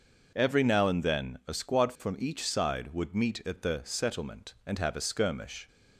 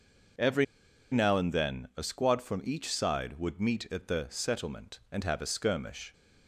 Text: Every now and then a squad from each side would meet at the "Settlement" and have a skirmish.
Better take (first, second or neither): first